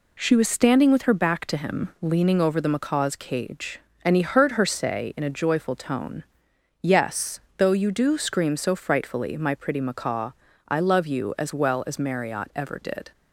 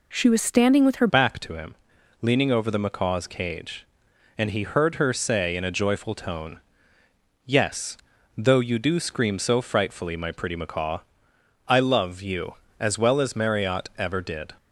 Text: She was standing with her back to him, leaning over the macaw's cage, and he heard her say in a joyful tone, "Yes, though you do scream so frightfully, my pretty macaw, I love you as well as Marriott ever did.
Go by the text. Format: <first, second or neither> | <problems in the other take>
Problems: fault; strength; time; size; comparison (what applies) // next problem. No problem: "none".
first | changes voice at "back"; from 1.0 s on; 13.5 s long